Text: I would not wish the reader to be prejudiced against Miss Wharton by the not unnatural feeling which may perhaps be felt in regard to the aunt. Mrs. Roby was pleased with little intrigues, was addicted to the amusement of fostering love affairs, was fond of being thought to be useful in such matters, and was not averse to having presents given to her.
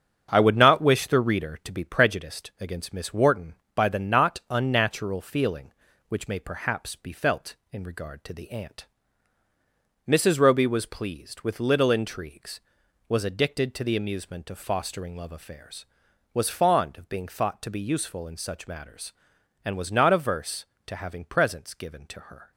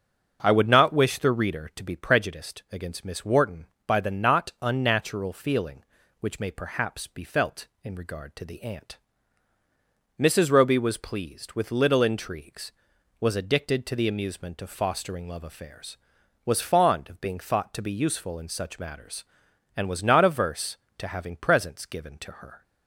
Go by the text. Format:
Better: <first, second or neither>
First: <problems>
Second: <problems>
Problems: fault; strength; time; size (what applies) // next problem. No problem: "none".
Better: second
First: gets quieter; throughout; 7 dB // starts louder than the rest; strong; until 1.3 s; 7.5 dB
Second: starts louder than the rest; until 1.4 s; 6.5 dB